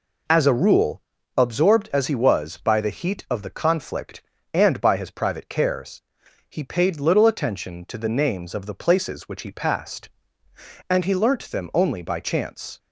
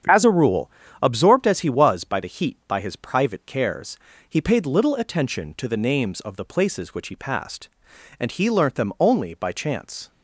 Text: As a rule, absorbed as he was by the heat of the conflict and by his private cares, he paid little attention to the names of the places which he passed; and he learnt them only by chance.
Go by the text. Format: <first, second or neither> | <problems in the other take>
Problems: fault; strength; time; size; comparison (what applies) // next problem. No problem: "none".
first | starts louder than the rest; strong; until 1.3 s; 8.5 dB // skips "of the conflict and"; at 2.6 s